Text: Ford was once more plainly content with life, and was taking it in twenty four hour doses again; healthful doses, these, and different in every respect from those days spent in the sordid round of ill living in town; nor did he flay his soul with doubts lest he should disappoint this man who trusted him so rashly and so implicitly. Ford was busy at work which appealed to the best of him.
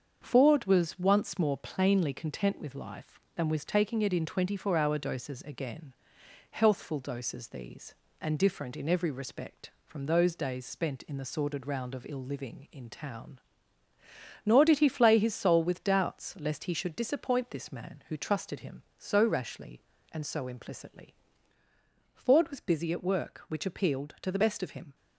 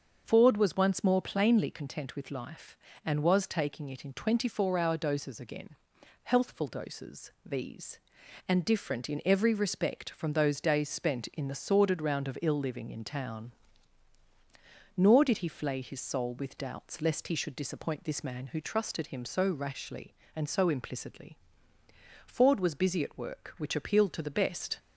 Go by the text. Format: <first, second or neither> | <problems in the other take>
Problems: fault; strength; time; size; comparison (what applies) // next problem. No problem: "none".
first | starts louder than the rest; until 1.2 s; 6.5 dB; also in the first // stops before "of him"; at 24.7 s